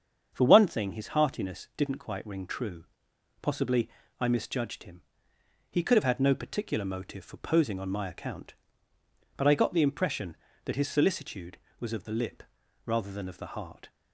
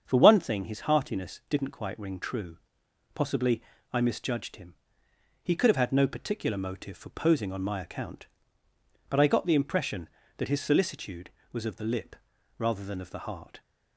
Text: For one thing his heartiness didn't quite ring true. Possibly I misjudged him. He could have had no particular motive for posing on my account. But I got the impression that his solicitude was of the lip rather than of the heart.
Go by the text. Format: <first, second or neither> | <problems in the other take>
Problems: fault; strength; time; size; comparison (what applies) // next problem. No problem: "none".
neither | starts louder than the rest; strong; the same in both // pauses between "Possibly" and "I"; slight; the same in both // pauses between "lip" and "rather"; the same in both